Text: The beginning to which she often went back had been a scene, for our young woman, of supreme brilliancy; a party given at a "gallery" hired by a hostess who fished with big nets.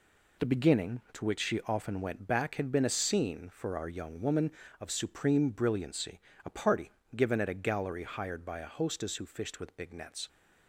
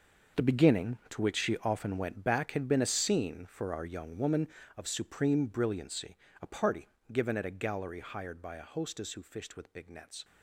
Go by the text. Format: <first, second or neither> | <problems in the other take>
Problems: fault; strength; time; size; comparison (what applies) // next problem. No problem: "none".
first | gets quieter; strong; throughout; 13.5 dB // pauses between "party" and "given"; slight; at 6.8 s; 0.24 s long; slight in the first